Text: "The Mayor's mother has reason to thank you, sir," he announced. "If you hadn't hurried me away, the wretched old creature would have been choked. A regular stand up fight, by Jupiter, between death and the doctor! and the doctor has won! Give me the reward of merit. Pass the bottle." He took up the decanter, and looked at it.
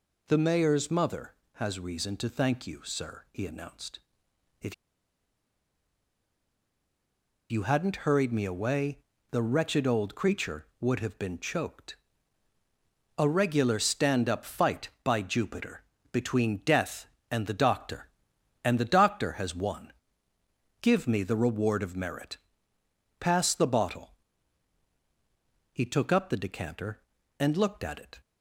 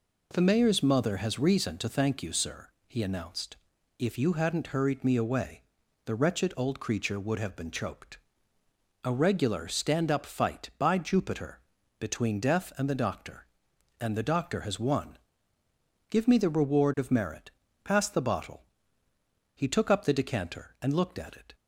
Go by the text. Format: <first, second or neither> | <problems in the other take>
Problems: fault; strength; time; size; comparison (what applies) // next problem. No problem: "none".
second | pauses between "If" and "you"; strong; at 4.7 s; 2.7 s long